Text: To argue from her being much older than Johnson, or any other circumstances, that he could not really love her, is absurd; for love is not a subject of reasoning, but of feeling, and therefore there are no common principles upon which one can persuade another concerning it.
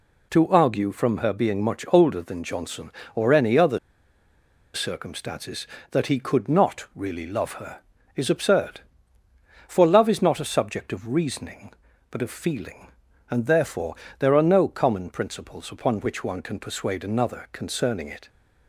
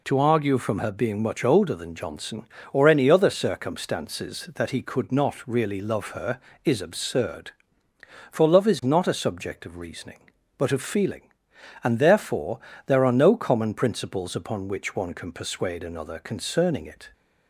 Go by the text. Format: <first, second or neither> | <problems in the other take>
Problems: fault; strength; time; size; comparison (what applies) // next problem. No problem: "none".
second | pauses between "other" and "circumstances"; noticeable; at 3.7 s; 0.95 s long // pauses between "therefore" and "there"; slight; at 13.9 s; 0.24 s long; slight in the second